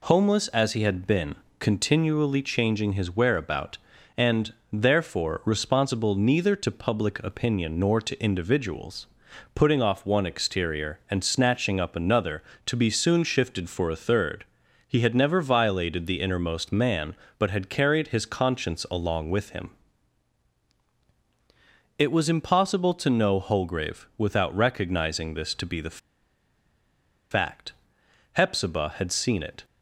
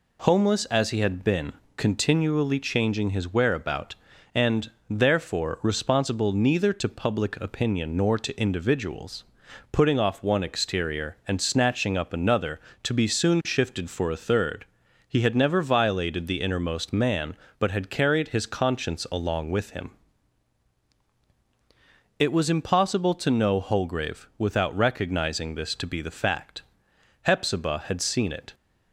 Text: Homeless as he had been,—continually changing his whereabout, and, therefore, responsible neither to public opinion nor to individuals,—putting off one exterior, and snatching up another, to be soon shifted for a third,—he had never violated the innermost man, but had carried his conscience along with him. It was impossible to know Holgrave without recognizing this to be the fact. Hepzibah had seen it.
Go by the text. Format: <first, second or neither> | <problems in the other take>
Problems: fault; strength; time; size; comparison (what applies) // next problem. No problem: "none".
second | pauses between "the" and "fact"; strong; at 25.9 s; 1.3 s long